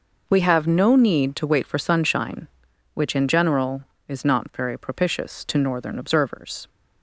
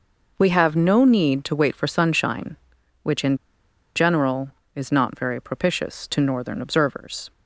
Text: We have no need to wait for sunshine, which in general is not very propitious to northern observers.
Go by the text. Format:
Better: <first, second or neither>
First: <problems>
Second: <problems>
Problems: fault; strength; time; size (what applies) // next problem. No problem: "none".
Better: first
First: none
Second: pauses between "in" and "general"; noticeable; at 3.3 s; 0.58 s long